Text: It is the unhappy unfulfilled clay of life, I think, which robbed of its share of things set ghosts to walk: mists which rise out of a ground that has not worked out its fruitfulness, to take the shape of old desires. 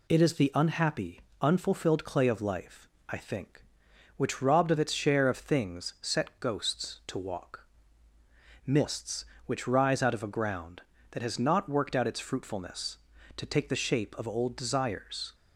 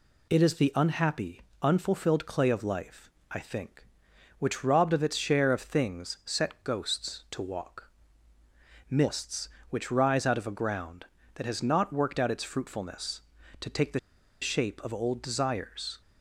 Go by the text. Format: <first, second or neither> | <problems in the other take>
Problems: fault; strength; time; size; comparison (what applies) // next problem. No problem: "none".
first | pauses between "unhappy" and "unfulfilled"; slight; at 1.4 s; 0.20 s long; slight in the first // pauses between "the" and "shape"; at 13.9 s; 0.43 s long